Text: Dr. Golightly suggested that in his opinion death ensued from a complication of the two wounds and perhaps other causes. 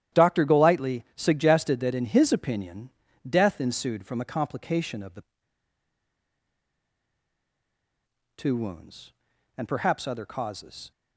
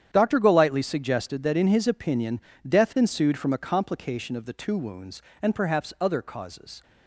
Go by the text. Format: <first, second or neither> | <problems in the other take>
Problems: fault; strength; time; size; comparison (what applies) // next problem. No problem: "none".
second | starts louder than the rest; strong; until 1.2 s; 11 dB; strong in the second // pauses between "opinion" and "death"; at 2.9 s; 0.38 s long; slight in the second // pauses between "the" and "two"; strong; at 5.2 s; 3.1 s long